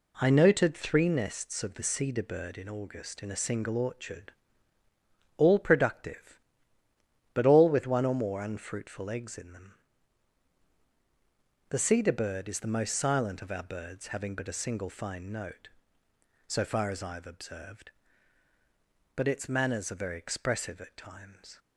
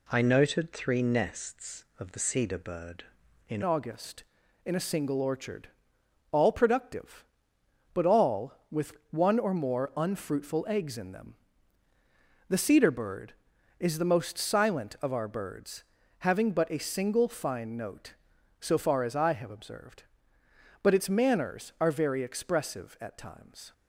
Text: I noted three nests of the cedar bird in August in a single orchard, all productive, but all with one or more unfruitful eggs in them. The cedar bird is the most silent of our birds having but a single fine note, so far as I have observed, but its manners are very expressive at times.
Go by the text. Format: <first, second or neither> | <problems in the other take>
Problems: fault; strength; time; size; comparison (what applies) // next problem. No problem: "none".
first | changes voice at "August"; from 3.6 s on; 20.1 s long // pauses between "with" and "one"; slight; at 8.9 s; 0.18 s long // pauses between "birds" and "having"; at 15.8 s; 0.38 s long